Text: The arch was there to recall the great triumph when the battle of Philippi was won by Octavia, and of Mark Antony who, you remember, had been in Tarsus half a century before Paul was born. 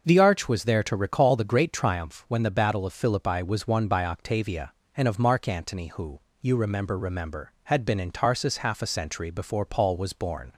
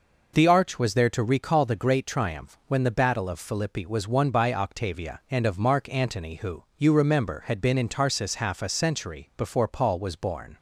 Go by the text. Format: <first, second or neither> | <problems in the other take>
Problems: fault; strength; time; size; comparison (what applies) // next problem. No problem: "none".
second | starts louder than the rest; until 1.0 s; 6 dB // says "remember" twice; at 6.9 s